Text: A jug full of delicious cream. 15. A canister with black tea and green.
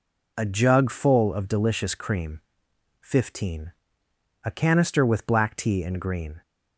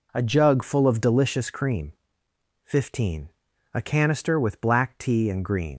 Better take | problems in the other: first | leaves "green" unfinished; at 5.7 s; 75 ms

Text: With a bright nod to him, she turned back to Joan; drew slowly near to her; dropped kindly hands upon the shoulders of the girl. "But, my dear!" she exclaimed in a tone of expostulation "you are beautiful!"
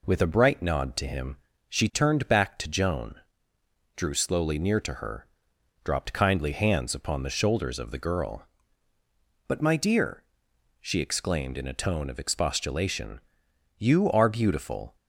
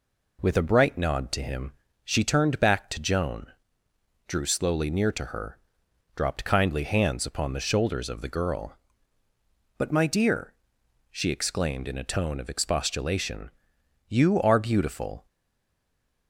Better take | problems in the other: first | pauses between "expostulation" and "you"; noticeable; at 13.4 s; 0.58 s long; noticeable in the first // stays silent after the last word; from 15.2 s on; 1.0 s long

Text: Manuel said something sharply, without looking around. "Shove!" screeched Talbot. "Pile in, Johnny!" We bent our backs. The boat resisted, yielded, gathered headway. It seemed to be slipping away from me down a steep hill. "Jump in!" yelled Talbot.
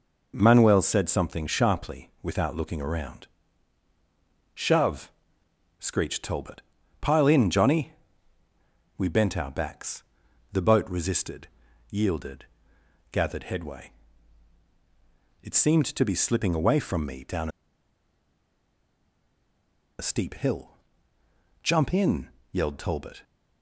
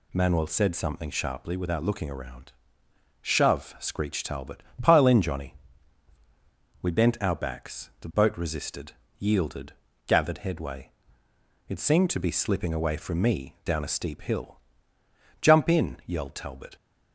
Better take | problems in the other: second | pauses between "down" and "a"; strong; at 17.4 s; 2.5 s long

